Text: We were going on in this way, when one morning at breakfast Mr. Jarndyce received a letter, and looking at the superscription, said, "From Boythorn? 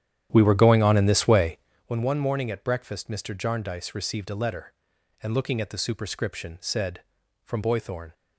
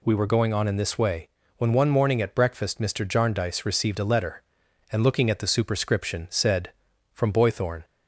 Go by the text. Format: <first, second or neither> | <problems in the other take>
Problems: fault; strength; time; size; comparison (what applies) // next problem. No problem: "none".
second | starts louder than the rest; strong; until 1.9 s; 10.5 dB